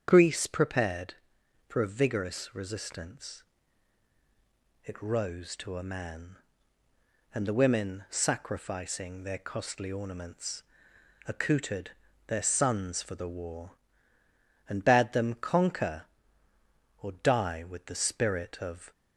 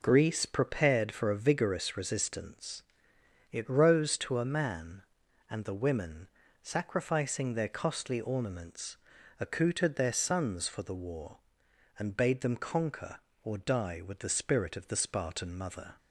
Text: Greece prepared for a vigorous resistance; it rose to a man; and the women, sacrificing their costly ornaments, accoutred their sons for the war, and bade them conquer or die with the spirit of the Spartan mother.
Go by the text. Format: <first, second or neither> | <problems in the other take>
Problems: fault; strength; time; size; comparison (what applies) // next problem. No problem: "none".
second | starts louder than the rest; strong; until 1.1 s; 8 dB // pauses between "accoutred" and "their"; slight; at 11.9 s; 0.34 s long // stops before "the Spartan mother"; at 18.9 s